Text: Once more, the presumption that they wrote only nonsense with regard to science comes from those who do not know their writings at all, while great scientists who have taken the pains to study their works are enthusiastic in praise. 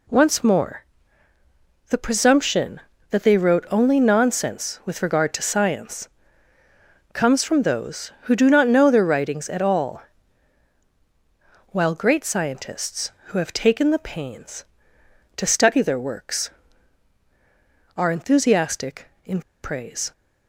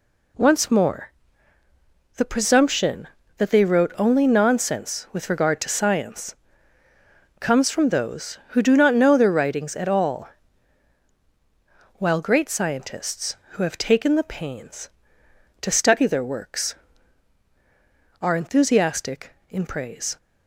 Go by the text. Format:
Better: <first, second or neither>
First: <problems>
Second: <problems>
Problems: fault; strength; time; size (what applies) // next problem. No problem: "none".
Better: second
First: pauses between "science" and "comes"; at 6.0 s; 1.0 s long // pauses between "in" and "praise"; slight; at 19.4 s; 0.20 s long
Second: pauses between "science" and "comes"; at 6.3 s; 1.0 s long